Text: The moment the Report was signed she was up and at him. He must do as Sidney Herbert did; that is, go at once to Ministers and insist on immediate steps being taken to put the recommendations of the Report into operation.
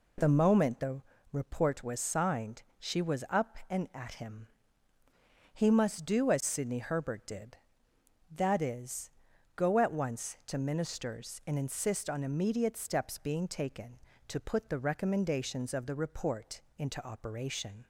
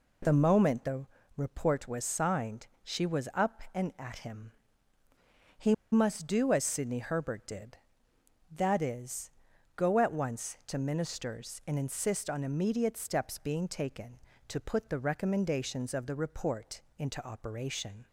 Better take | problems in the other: first | pauses between "the" and "Report"; slight; at 1.0 s; 0.30 s long; slight in the first // pauses between "He" and "must"; slight; at 5.7 s; 0.17 s long // pauses between "Report" and "into"; slight; at 16.8 s; 0.16 s long; slight in the first

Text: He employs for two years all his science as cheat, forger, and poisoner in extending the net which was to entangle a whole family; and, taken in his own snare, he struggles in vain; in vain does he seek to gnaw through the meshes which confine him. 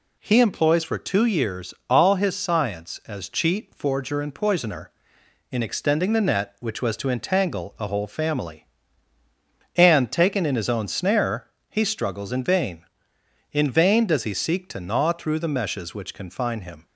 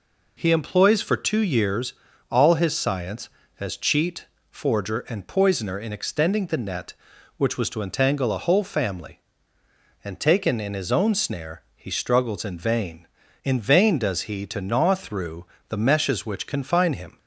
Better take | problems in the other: first | pauses between "years" and "all"; slight; at 1.9 s; 0.36 s long; slight in the first // skips "seek"; at 14.4 s // pauses between "through" and "the"; slight; at 15.4 s; 0.26 s long

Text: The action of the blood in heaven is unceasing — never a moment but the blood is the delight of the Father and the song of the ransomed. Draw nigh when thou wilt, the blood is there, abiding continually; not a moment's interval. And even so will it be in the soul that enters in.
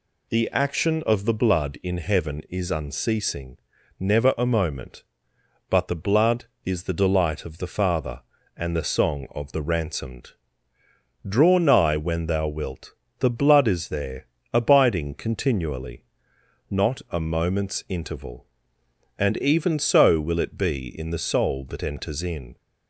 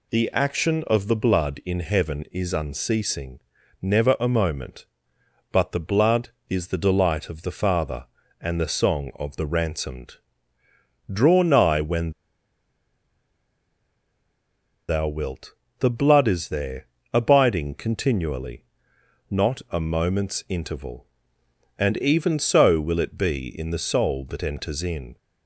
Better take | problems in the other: first | pauses between "when" and "thou"; strong; at 12.1 s; 2.7 s long

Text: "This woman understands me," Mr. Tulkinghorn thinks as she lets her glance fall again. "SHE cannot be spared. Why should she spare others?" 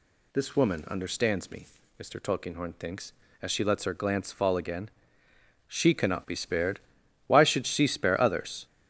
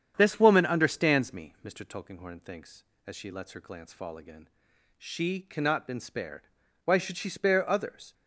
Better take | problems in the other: first | starts louder than the rest; strong; until 1.1 s; 8.5 dB // says "been" for "be"; at 5.8 s

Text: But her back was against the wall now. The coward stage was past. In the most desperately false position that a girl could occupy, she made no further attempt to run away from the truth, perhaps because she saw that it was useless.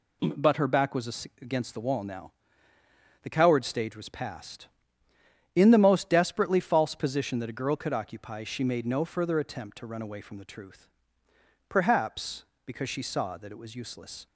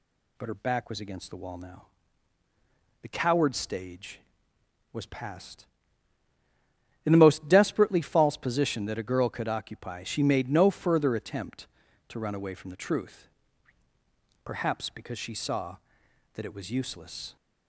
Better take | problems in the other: neither | none

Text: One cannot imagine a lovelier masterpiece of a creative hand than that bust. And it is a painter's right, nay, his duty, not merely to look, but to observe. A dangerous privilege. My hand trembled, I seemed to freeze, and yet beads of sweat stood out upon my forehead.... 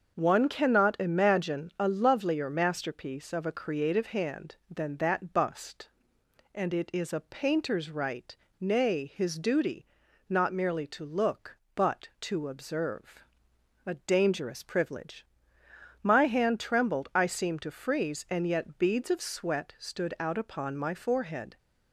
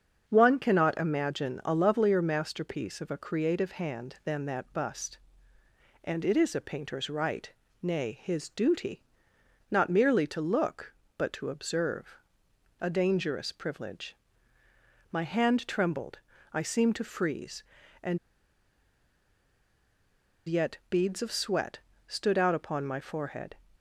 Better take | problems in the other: first | starts louder than the rest; until 1.2 s; 7 dB; also in the first // pauses between "and" and "yet"; strong; at 18.1 s; 2.3 s long // pauses between "sweat" and "stood"; slight; at 21.8 s; 0.26 s long

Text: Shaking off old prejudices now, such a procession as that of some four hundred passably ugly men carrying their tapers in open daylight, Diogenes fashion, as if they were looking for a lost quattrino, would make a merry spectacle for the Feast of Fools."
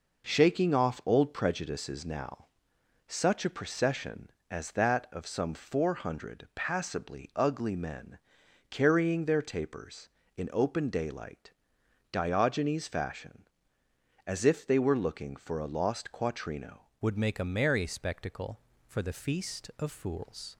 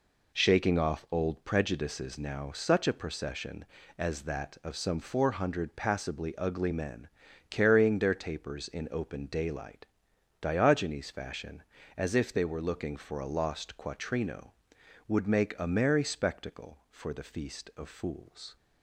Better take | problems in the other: second | pauses between "men" and "carrying"; noticeable; at 8.1 s; 0.54 s long; also in the second // changes voice at "would"; from 17.0 s on; 3.5 s long

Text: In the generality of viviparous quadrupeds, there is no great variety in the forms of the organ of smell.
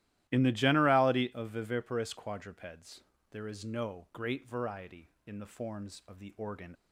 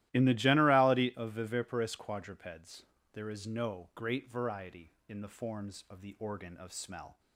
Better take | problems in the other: second | starts louder than the rest; strong; until 1.2 s; 14.5 dB; strong in the second // stops before "of smell"; at 6.7 s

